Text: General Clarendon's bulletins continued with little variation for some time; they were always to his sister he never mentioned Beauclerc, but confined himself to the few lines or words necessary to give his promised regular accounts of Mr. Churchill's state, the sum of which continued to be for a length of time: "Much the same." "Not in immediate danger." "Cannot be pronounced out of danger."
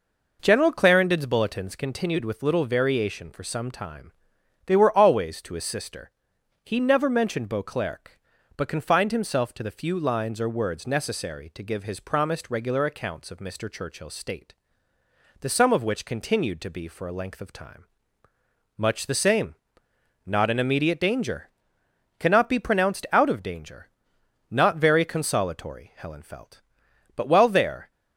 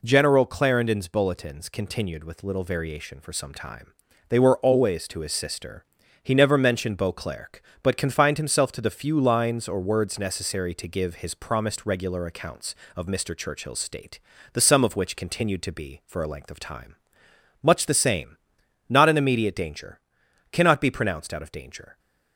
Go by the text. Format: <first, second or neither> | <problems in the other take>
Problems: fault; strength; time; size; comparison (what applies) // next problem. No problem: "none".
second | pauses between "sister" and "he"; noticeable; at 6.1 s; 0.52 s long; also in the second // goes on to say "Not very consolatory Helen felt But while there"; strong; from 24.4 s on; 3.4 s long